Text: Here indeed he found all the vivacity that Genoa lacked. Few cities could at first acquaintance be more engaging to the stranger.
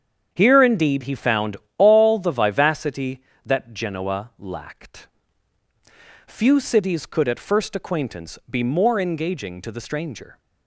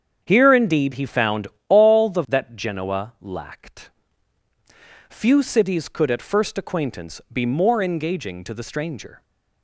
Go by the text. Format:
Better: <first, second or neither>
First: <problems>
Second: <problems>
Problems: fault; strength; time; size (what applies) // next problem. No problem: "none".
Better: first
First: starts louder than the rest; strong; until 1.3 s; 8 dB // pauses between "found" and "all"; slight; at 1.5 s; 0.20 s long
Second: starts louder than the rest; strong; until 1.2 s; 7.5 dB // pauses between "found" and "all"; slight; at 1.4 s; 0.20 s long // skips "vivacity"; at 2.2 s